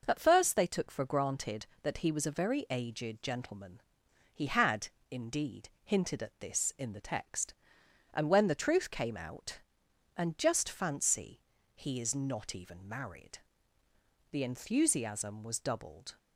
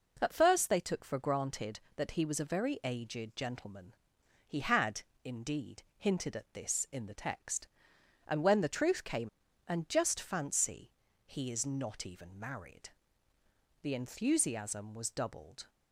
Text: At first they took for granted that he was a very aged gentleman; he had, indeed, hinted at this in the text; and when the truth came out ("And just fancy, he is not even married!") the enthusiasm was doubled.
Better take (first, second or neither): first